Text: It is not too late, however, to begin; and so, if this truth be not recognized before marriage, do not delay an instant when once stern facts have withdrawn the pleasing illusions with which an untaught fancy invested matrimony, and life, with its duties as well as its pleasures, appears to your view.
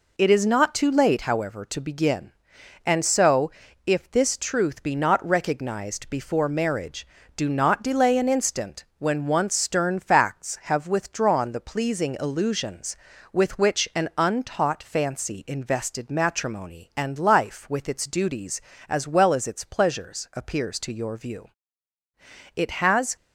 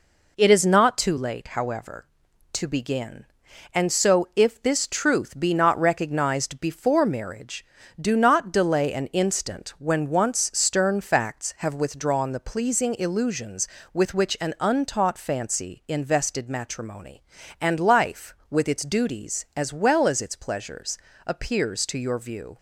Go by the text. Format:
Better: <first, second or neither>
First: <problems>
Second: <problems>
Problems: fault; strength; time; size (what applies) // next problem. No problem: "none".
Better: second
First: goes on to say "It has"; noticeable; from 22.5 s on; 0.62 s long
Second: none